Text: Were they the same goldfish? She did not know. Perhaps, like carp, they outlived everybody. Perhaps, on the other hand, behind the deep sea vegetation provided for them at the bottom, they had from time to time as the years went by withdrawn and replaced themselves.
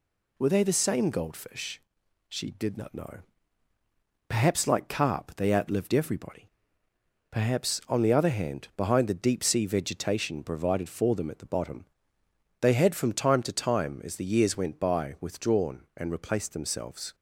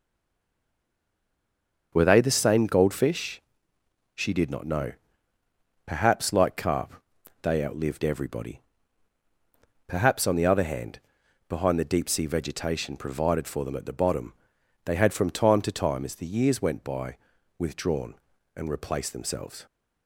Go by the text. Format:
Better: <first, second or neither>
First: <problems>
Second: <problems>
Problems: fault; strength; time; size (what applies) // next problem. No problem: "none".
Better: first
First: none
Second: stays silent before the first word; noticeable; until 1.9 s; 1.9 s long // starts louder than the rest; until 2.9 s; 6.5 dB // pauses between "by" and "withdrawn"; at 17.1 s; 0.42 s long